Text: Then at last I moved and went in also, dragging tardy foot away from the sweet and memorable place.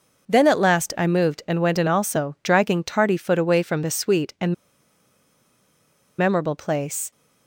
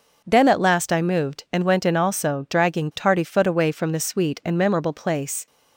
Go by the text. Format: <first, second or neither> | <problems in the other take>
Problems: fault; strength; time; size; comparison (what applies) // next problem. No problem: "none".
second | pauses between "and" and "memorable"; strong; at 4.5 s; 1.6 s long